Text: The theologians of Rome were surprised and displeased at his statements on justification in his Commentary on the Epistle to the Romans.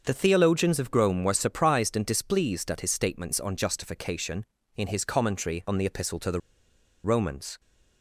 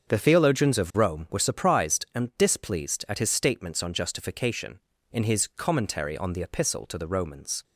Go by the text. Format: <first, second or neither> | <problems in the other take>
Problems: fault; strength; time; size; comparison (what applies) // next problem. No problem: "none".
second | starts louder than the rest; until 1.0 s; 6.5 dB; also in the second // pauses between "the" and "Romans"; noticeable; at 6.4 s; 0.63 s long